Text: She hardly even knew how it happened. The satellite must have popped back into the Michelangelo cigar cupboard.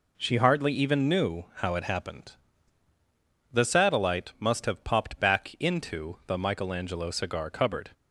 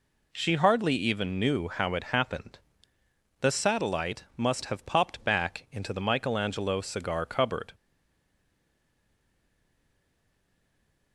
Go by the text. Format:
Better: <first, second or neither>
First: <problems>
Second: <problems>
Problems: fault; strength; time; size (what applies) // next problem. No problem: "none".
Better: first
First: none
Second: stays silent after the last word; strong; from 7.7 s on; 3.4 s long